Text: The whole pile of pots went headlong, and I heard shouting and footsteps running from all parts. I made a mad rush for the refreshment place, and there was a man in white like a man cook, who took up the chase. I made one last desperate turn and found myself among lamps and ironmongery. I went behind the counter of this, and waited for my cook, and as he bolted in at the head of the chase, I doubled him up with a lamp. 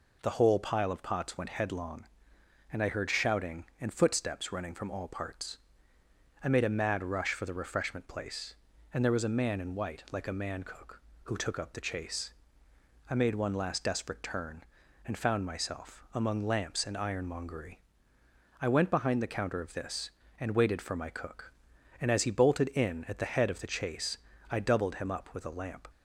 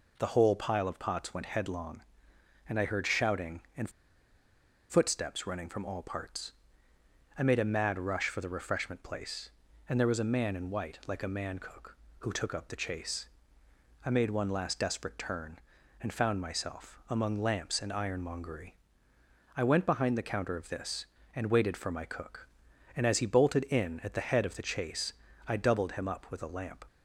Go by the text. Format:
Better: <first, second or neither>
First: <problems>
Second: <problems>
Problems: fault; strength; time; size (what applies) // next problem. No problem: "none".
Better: first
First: none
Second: pauses between "and" and "footsteps"; at 3.8 s; 1.0 s long